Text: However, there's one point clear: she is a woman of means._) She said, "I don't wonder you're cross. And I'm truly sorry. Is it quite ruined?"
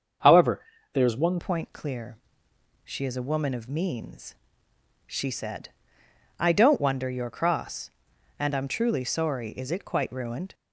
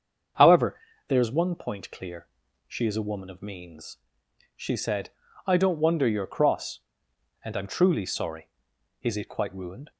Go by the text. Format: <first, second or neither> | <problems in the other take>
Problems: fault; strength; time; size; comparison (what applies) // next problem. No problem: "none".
second | starts louder than the rest; until 1.5 s; 6.5 dB; also in the second // changes voice at "point"; from 1.3 s on; 9.2 s long